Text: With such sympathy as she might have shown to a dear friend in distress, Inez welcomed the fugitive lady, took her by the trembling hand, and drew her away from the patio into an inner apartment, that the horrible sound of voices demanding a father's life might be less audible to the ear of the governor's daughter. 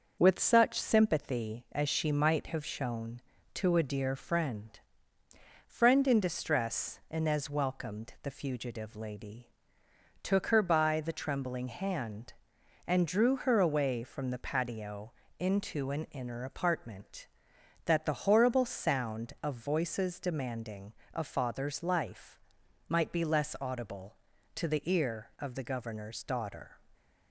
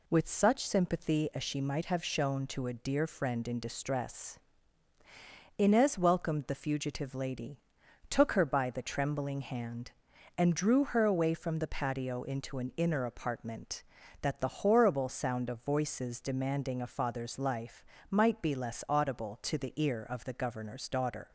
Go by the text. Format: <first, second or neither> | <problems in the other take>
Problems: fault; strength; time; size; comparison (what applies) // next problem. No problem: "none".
second | starts louder than the rest; noticeable; until 1.2 s; 6 dB // says "friend" twice; at 5.6 s // pauses between "patio" and "into"; slight; at 15.1 s; 0.26 s long // pauses between "demanding" and "a"; slight; at 20.9 s; 0.20 s long // pauses between "life" and "might"; noticeable; at 22.4 s; 0.48 s long; slight in the second